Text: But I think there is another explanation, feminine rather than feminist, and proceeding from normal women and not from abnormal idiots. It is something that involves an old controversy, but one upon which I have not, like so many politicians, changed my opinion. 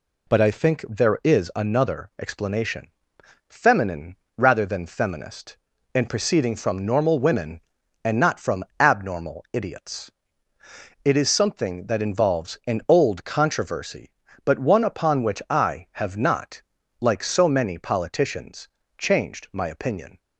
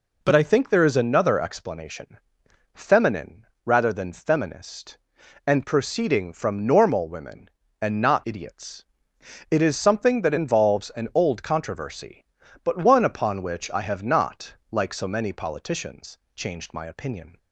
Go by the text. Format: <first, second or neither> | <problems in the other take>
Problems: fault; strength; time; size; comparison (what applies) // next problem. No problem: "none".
first | pauses between "feminine" and "rather"; slight; at 3.4 s; 0.18 s long; slight in the first // skips "from abnormal"; at 8.2 s